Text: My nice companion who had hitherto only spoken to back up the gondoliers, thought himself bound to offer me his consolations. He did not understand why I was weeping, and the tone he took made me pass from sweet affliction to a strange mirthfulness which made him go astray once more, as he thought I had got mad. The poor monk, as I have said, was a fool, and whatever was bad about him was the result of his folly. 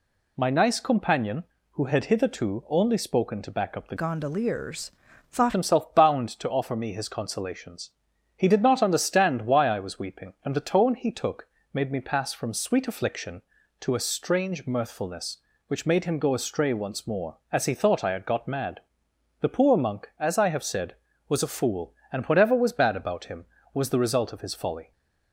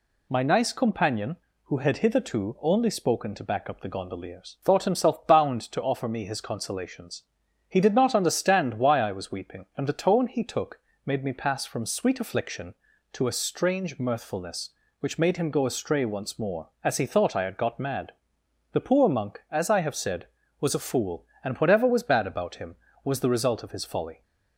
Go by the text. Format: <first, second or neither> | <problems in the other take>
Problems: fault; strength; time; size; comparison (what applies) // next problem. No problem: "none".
second | changes voice from "gondoliers" to "thought"; from 3.9 to 5.5 s; 1.6 s long // pauses between "took" and "made"; slight; at 11.4 s; 0.26 s long; slight in the second